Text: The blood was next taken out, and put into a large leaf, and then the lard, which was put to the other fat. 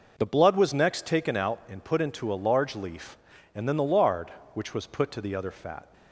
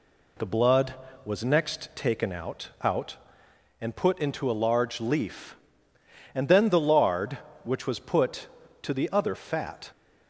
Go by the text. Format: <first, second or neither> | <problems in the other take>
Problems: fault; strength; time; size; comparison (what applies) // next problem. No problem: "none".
first | says "out" twice; at 2.8 s